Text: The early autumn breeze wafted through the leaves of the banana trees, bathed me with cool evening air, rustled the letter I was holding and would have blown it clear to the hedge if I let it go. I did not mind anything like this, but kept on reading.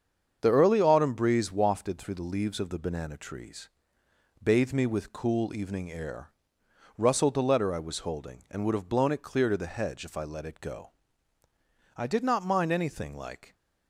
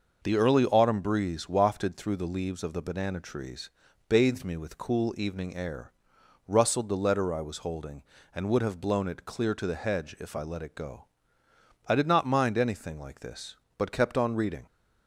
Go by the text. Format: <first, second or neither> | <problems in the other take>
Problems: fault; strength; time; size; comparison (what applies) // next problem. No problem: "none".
second | starts louder than the rest; strong; until 1.4 s; 7 dB // stops before "this but kept on reading"; at 13.5 s